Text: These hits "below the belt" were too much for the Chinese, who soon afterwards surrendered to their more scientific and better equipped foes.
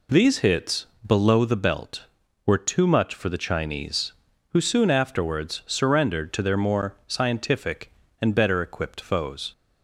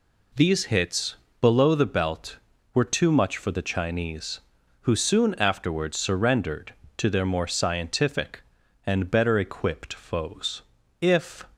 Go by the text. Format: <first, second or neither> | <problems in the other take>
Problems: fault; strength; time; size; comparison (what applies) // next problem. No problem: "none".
first | pauses between "hits" and "below"; slight; at 1.1 s; 0.28 s long; slight in the first // goes on to say "If"; slight; from 10.9 s on; 0.46 s long